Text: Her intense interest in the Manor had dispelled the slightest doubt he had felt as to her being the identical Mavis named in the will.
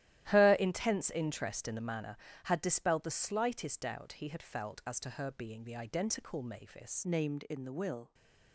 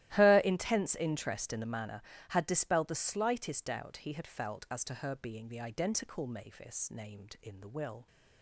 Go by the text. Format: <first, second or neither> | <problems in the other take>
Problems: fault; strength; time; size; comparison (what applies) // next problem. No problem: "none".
second | starts louder than the rest; strong; until 1.3 s; 13.5 dB; strong in the second // changes voice at "named"; from 7.0 s on; 1.1 s long